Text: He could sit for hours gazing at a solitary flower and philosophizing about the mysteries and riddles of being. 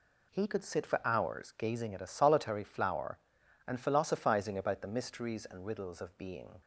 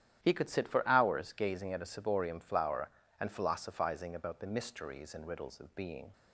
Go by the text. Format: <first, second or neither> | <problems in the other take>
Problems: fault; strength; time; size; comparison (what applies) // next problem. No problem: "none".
first | starts louder than the rest; strong; until 1.2 s; 11.5 dB // says "ciborium" for "solitary"; at 1.8 s